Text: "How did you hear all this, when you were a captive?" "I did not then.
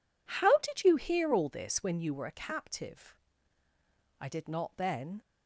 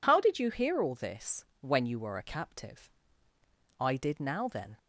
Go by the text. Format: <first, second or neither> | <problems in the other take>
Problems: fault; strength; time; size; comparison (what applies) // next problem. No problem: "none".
first | says "now" for "not"; at 4.1 s